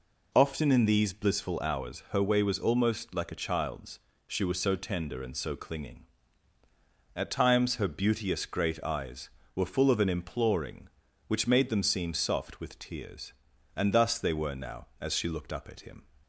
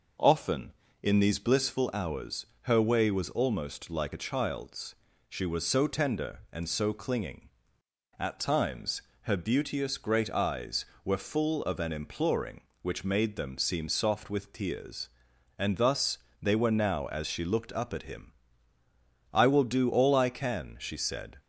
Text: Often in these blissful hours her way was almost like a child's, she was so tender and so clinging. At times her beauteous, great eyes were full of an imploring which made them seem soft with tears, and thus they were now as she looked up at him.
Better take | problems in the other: first | pauses between "hours" and "her"; slight; at 2.4 s; 0.16 s long // pauses between "times" and "her"; slight; at 9.0 s; 0.20 s long // pauses between "thus" and "they"; slight; at 16.1 s; 0.24 s long // goes on to say "I will do all I can she said"; strong; from 19.3 s on; 2.0 s long

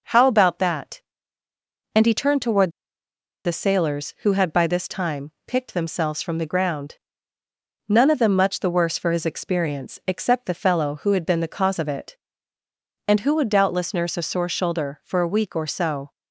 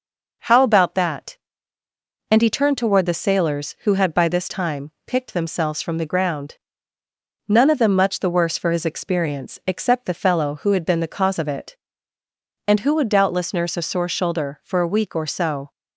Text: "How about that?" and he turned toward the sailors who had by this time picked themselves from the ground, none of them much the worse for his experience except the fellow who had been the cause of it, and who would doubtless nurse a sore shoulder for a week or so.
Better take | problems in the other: second | pauses between "toward" and "the"; noticeable; at 2.7 s; 0.73 s long // pauses between "time" and "picked"; slight; at 5.3 s; 0.16 s long; slight in the second

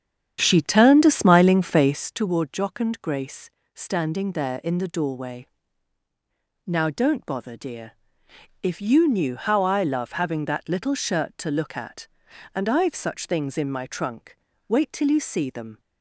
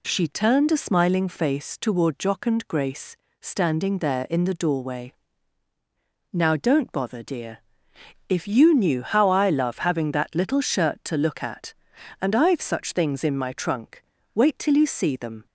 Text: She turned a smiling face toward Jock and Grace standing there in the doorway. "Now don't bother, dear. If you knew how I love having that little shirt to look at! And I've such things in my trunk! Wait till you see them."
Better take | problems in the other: second | starts louder than the rest; strong; until 2.3 s; 9 dB // pauses between "Grace" and "standing"; slight; at 3.4 s; 0.26 s long; slight in the second

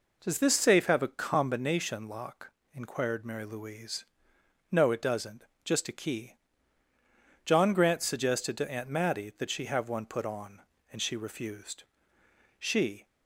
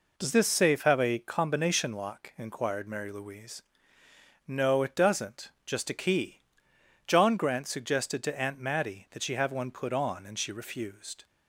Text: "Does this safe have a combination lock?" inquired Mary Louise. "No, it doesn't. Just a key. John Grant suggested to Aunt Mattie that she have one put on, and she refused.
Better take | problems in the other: second | goes on to say "She"; slight; from 12.5 s on; 0.48 s long

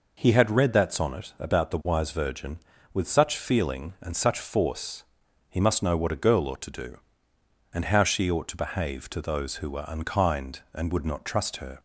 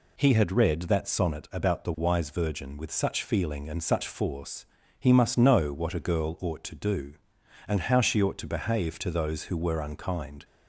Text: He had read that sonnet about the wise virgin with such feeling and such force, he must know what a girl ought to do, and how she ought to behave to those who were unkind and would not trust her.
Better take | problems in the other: first | stops before "and would not trust her"; at 10.4 s

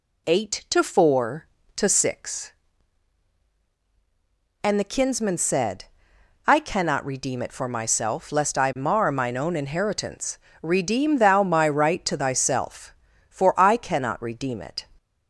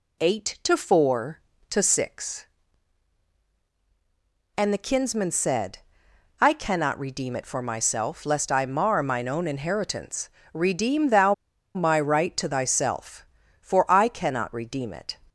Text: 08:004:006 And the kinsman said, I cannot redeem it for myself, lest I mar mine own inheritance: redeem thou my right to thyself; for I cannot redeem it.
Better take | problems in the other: first | pauses between "thou" and "my"; at 11.3 s; 0.41 s long

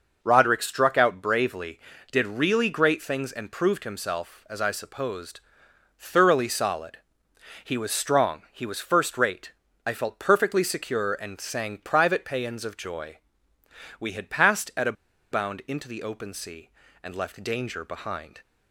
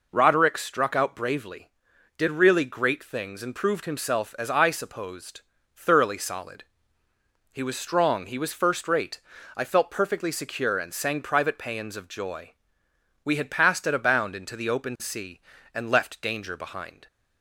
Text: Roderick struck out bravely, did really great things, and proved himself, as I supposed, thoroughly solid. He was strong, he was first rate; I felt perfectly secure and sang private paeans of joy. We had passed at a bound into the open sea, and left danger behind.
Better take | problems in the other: second | pauses between "a" and "bound"; at 14.9 s; 0.38 s long

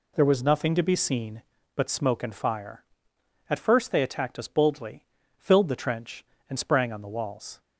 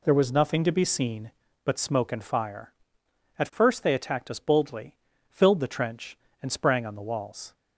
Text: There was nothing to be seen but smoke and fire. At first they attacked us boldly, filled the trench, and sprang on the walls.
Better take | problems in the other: neither | none

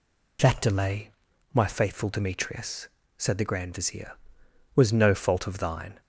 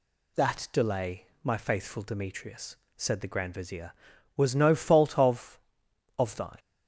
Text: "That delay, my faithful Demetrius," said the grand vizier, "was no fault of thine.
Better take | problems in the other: first | says "of" twice; at 6.1 s

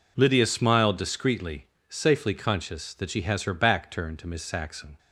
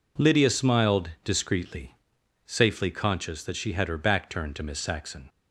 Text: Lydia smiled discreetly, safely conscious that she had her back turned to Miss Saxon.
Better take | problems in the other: second | says "has" for "had"; at 3.2 s

